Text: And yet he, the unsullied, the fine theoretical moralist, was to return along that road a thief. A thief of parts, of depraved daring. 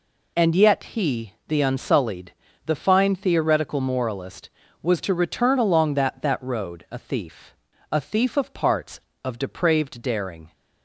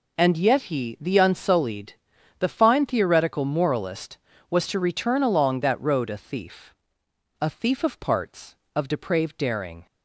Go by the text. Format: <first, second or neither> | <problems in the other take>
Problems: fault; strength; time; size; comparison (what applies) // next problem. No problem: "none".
second | says "that" twice; at 6.2 s